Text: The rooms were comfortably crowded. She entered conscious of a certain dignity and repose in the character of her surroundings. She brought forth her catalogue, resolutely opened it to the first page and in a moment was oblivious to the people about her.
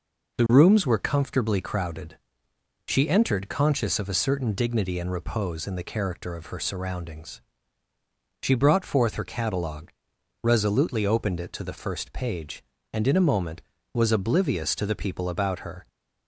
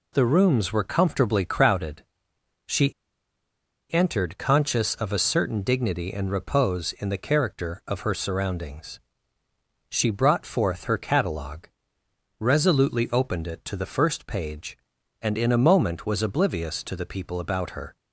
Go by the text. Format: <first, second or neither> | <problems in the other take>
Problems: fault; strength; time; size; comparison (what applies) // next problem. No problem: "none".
first | pauses between "She" and "entered"; at 2.9 s; 0.99 s long